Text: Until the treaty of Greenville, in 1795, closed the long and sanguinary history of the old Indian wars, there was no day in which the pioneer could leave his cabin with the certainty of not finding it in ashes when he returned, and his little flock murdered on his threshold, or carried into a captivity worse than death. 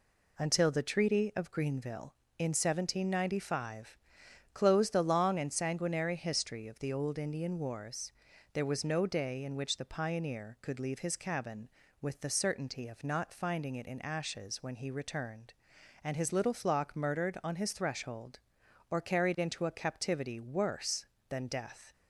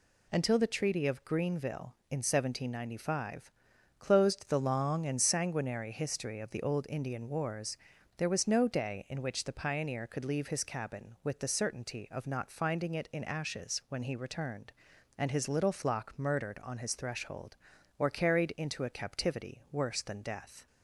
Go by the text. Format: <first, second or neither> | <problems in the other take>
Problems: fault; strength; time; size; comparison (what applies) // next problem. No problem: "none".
neither | none